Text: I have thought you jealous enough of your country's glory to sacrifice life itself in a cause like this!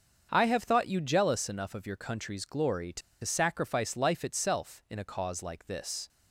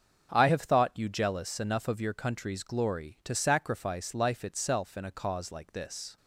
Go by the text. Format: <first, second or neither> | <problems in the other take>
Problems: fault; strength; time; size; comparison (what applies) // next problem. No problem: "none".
second | starts louder than the rest; until 1.3 s; 7 dB; also in the second // pauses between "to" and "sacrifice"; slight; at 3.0 s; 0.23 s long